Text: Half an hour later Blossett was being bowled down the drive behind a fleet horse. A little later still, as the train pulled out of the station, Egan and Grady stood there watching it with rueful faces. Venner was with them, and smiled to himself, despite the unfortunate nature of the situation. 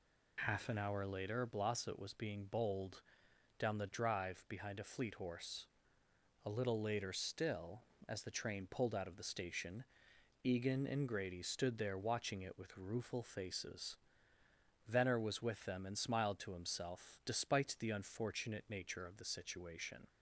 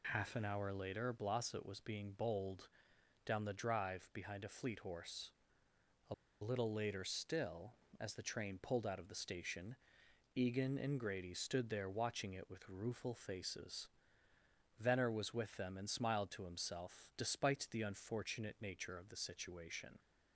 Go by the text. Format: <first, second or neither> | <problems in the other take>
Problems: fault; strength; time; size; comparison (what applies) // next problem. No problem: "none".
first | pauses between "bowled" and "down"; noticeable; at 2.6 s; 0.58 s long; noticeable in the first // pauses between "A" and "little"; slight; at 6.1 s; 0.27 s long